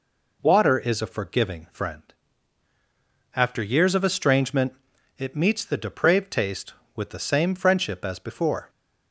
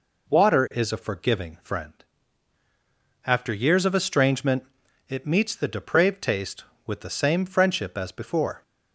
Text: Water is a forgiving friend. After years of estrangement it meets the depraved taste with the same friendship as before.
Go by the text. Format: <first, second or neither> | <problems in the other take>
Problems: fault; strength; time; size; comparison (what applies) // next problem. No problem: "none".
neither | pauses between "estrangement" and "it"; the same in both